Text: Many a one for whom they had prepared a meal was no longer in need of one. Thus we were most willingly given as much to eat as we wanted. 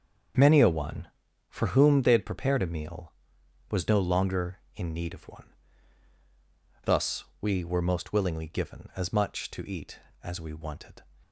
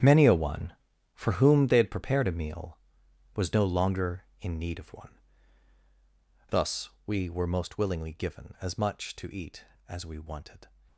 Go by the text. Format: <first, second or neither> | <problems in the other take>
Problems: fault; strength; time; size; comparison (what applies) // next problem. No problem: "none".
first | gets quieter; strong; throughout; 14.5 dB // starts louder than the rest; strong; until 1.4 s; 9 dB; also in the first // pauses between "Thus" and "we"; slight; at 6.8 s; 0.16 s long; slight in the first